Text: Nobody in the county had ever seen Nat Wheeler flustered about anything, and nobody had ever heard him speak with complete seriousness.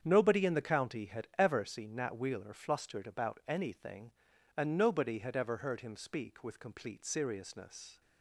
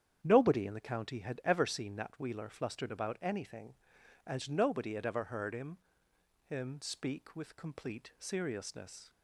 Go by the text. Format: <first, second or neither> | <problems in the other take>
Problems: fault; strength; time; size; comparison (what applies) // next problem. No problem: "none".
first | starts louder than the rest; strong; until 1.2 s; 9 dB; strong in the first // says "him" twice; at 6.4 s